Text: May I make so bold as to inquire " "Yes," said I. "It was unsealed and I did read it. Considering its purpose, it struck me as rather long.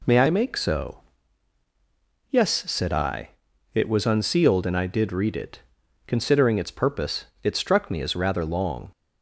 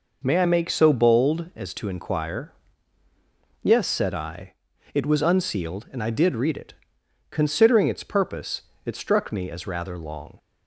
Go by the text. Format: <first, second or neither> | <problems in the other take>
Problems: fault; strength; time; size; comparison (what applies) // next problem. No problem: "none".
second | skips "bold as to inquire"; at 1.3 s